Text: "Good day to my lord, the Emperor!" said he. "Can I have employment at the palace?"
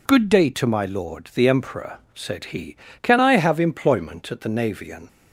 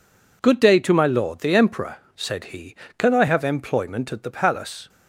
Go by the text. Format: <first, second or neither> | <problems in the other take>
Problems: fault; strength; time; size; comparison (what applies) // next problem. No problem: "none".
second | says "navian" for "palace"; at 4.4 s